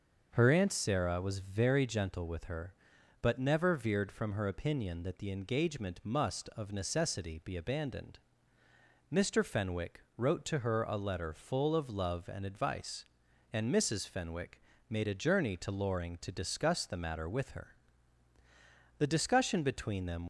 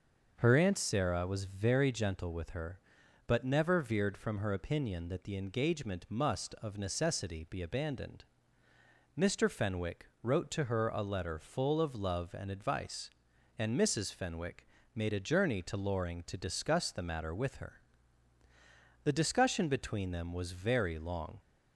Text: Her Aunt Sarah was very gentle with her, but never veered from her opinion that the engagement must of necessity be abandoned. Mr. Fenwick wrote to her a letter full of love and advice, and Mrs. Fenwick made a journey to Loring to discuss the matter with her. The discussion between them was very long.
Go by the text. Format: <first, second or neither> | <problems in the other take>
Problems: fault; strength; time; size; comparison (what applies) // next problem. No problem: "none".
second | starts louder than the rest; noticeable; until 1.3 s; 6 dB; noticeable in the second // pauses between "Fenwick" and "wrote"; slight; at 10.0 s; 0.16 s long; slight in the second // pauses between "Fenwick" and "made"; slight; at 14.6 s; 0.28 s long; slight in the second // stops before "was very long"; at 20.2 s